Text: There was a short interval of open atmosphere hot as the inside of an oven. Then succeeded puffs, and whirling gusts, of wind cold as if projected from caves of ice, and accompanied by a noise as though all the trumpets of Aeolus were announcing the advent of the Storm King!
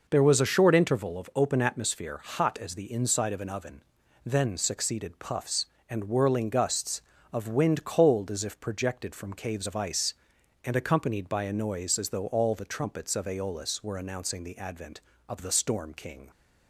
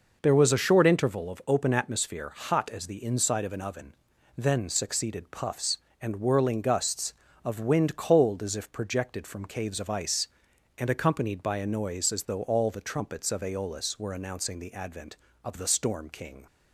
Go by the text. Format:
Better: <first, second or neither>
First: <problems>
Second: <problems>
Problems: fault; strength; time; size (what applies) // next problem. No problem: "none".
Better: neither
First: none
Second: none